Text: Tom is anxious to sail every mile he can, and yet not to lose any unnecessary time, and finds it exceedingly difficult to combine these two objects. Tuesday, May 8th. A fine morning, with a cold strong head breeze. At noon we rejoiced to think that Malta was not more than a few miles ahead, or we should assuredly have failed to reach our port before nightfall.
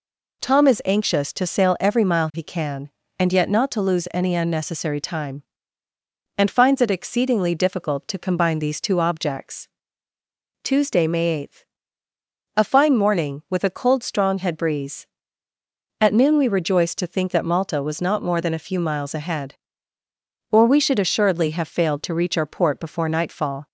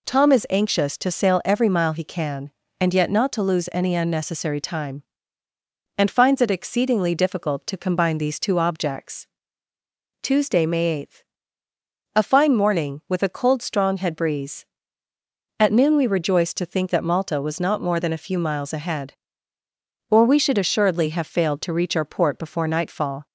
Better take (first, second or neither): neither